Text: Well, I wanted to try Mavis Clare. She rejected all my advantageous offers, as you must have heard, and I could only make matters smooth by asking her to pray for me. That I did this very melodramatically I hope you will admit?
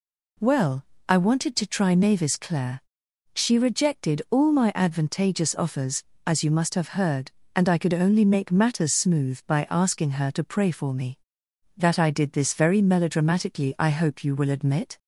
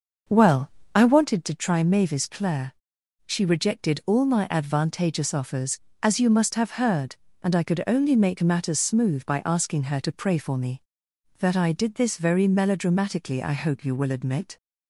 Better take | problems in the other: first | starts louder than the rest; noticeable; until 1.3 s; 6 dB

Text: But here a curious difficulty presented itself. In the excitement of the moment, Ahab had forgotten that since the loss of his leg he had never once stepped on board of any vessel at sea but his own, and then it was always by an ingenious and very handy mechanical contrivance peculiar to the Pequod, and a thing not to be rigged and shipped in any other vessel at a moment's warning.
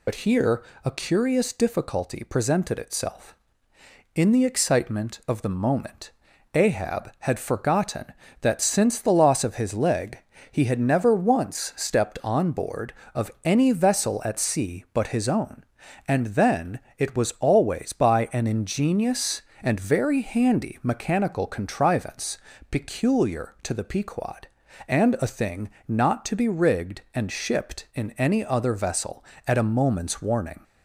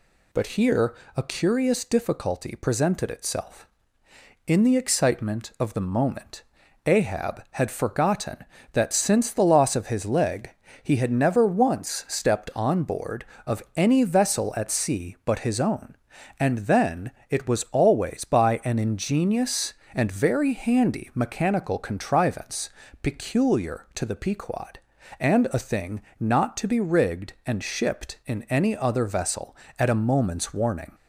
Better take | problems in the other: second | loses the start of "But"; at 0.0 s; 65 ms // pauses between "here" and "a"; slight; at 0.6 s; 0.22 s long; slight in the second // pauses between "leg" and "he"; slight; at 10.1 s; 0.32 s long; slight in the second // pauses between "then" and "it"; slight; at 16.8 s; 0.16 s long; slight in the second // pauses between "contrivance" and "peculiar"; slight; at 22.3 s; 0.32 s long; slight in the second // pauses between "thing" and "not"; slight; at 25.6 s; 0.18 s long; slight in the second

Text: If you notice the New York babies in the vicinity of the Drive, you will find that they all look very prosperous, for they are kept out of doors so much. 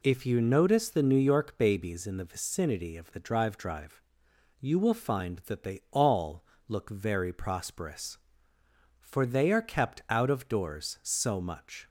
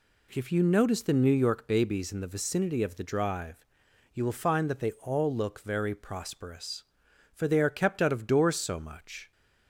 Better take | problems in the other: second | says "Drive" twice; at 3.5 s // pauses between "all" and "look"; slight; at 6.4 s; 0.24 s long

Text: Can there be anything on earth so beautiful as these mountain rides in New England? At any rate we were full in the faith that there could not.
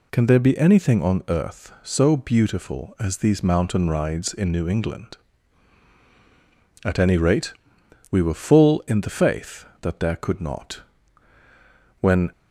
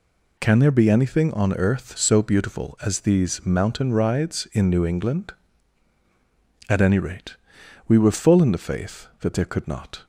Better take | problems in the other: second | pauses between "rate" and "we"; noticeable; at 7.5 s; 0.56 s long; noticeable in the second // goes on to say "When"; slight; from 11.9 s on; 0.32 s long

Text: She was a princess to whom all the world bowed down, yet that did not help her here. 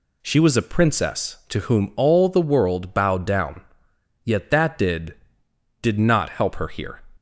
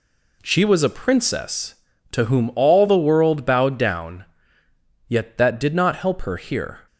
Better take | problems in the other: second | says "did" twice; at 5.8 s

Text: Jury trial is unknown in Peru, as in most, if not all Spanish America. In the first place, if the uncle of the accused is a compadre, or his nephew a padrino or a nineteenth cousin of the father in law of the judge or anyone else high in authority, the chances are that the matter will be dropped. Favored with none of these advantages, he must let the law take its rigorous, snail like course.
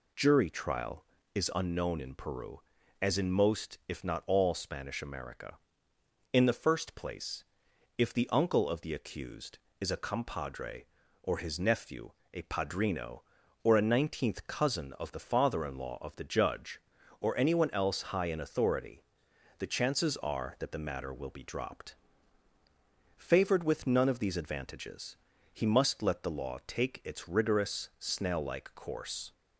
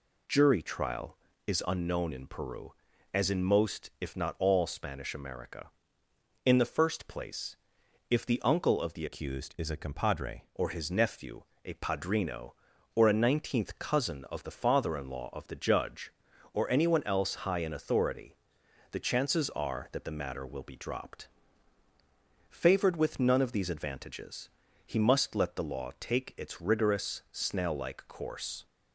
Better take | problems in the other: first | changes voice from "accused" to "compadre"; from 9.0 to 10.4 s; 1.4 s long // pauses between "nephew" and "a"; slight; at 11.4 s; 0.22 s long; slight in the first

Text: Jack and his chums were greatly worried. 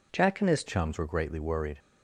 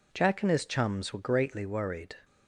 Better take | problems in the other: second | changes voice at "chums"; from 0.6 s on; 1.1 s long

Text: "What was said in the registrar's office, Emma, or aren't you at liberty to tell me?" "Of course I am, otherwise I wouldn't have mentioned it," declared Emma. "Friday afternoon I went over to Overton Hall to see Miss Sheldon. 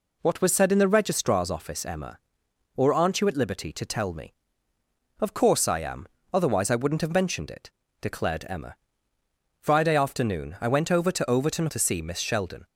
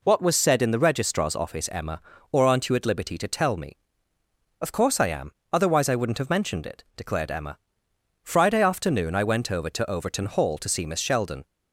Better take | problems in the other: second | skips "Hall"; at 11.6 s

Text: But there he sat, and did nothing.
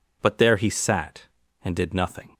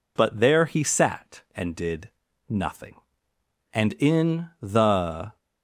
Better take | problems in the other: first | pauses between "did" and "nothing"; noticeable; at 2.0 s; 0.48 s long // goes on to say "And in the"; from 3.7 s on; 1.6 s long

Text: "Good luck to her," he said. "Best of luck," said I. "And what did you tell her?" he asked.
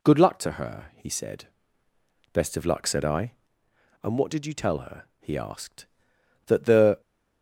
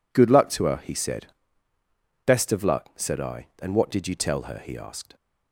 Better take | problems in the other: second | goes on to say "That the"; from 6.4 s on; 0.54 s long

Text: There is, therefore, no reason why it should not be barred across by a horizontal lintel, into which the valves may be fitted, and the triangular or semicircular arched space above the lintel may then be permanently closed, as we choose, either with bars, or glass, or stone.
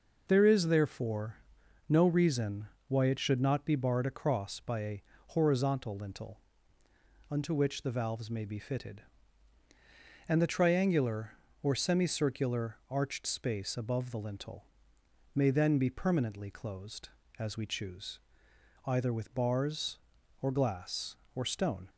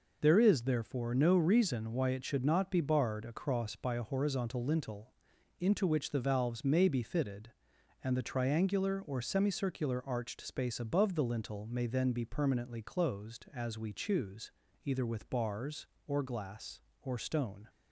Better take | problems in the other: second | pauses between "reason" and "why"; slight; at 2.6 s; 0.20 s long // pauses between "a" and "horizontal"; slight; at 5.0 s; 0.26 s long // says "unto" for "into"; at 7.2 s // pauses between "lintel" and "may"; noticeable; at 14.6 s; 0.70 s long

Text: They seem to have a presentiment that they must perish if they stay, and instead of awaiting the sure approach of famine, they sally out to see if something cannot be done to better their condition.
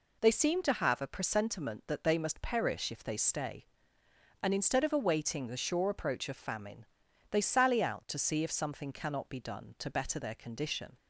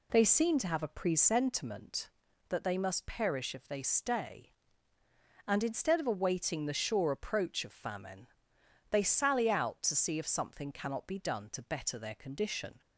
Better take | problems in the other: neither | none

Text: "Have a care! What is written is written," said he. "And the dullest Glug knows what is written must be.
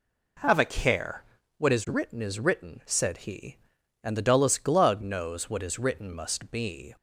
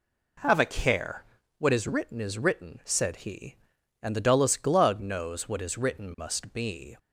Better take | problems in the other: neither | none

